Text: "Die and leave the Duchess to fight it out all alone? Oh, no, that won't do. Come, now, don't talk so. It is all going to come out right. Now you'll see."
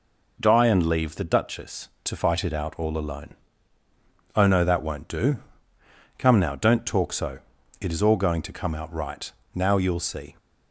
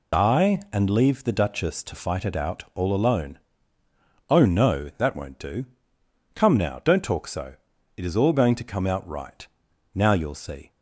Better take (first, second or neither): first